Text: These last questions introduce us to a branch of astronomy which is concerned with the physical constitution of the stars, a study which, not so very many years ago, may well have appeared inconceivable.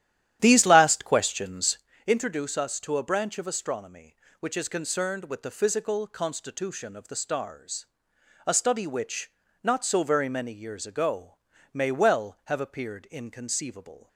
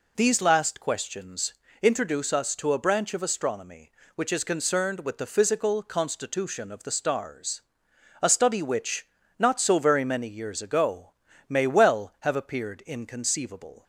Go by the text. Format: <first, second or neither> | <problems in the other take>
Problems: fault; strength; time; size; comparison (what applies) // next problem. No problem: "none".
second | starts louder than the rest; strong; until 1.9 s; 11.5 dB // pauses between "questions" and "introduce"; slight; at 1.7 s; 0.28 s long; slight in the second